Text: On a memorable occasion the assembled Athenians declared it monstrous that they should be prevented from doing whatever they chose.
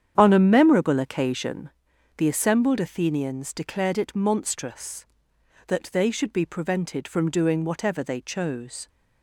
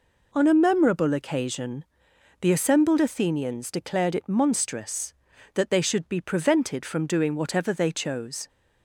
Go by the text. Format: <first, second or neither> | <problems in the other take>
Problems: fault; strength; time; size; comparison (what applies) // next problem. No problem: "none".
second | starts louder than the rest; strong; until 1.8 s; 8.5 dB // pauses between "occasion" and "the"; noticeable; at 1.6 s; 0.48 s long; noticeable in the second